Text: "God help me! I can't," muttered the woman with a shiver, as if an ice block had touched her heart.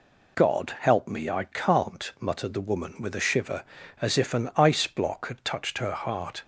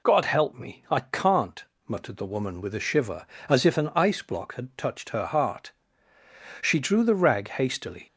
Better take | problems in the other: first | goes on to say "She drew the rag hastily"; from 6.6 s on; 1.4 s long

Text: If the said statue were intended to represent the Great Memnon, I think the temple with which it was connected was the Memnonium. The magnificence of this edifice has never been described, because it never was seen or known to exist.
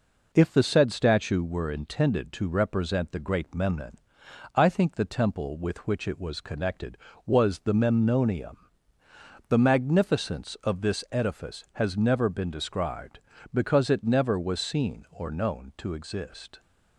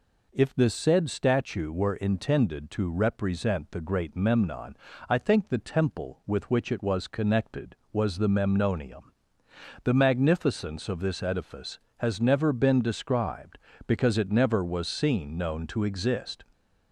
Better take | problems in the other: first | skips "or"; at 15.3 s

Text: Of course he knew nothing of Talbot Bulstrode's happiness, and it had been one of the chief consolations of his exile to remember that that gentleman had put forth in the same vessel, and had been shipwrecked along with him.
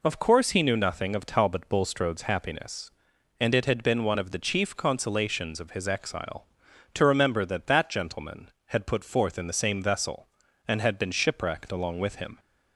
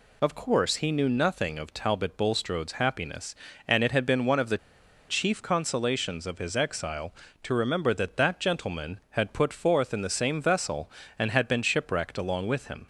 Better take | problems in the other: first | pauses between "the" and "chief"; noticeable; at 4.5 s; 0.50 s long

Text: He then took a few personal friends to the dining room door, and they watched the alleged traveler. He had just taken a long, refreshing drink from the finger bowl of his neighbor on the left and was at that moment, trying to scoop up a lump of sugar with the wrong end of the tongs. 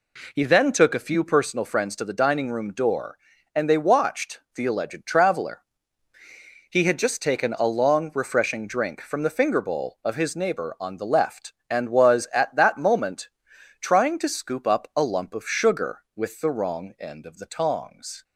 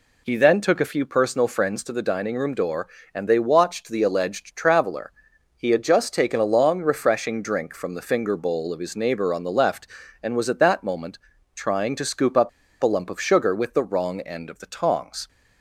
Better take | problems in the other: first | pauses between "up" and "a"; slight; at 12.4 s; 0.32 s long

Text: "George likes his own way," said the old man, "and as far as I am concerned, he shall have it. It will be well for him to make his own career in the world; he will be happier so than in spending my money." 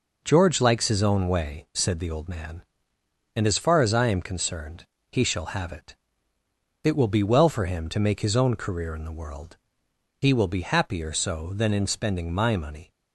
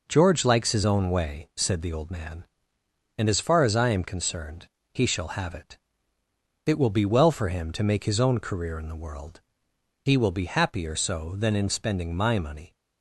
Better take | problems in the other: neither | none

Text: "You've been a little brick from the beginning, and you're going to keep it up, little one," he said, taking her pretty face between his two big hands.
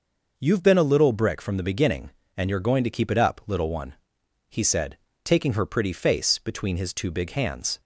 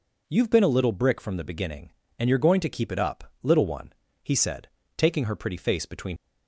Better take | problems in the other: first | stops before "his two big hands"; at 6.1 s

